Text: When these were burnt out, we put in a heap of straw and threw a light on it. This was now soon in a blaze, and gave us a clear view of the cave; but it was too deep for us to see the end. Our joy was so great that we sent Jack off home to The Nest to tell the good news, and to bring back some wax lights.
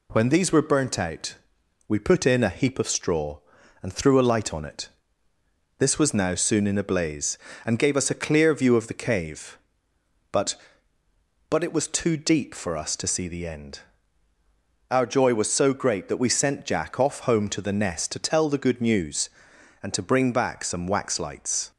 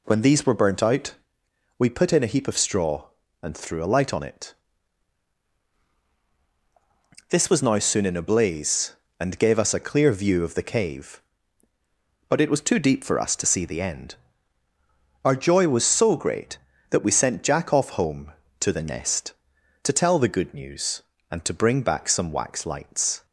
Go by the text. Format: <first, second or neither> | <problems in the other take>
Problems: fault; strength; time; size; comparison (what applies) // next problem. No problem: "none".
second | says "but" twice; at 11.4 s